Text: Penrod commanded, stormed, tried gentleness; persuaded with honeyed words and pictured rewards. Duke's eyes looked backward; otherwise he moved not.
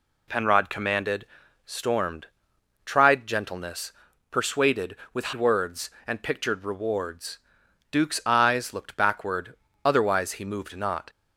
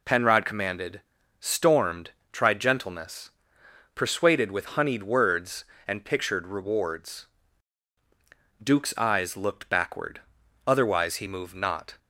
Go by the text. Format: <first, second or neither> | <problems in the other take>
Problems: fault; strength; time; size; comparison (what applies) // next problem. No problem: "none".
second | skips "honeyed"; at 5.3 s